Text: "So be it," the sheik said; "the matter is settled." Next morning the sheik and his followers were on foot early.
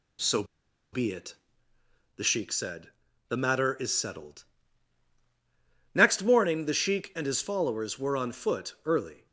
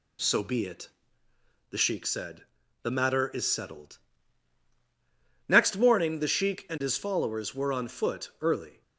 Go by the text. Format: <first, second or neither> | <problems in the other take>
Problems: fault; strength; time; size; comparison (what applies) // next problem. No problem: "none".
second | pauses between "So" and "be"; noticeable; at 0.4 s; 0.48 s long